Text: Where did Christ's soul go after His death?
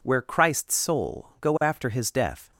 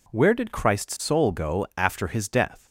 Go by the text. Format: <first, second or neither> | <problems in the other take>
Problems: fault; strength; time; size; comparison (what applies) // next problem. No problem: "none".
second | skips "did"; at 0.2 s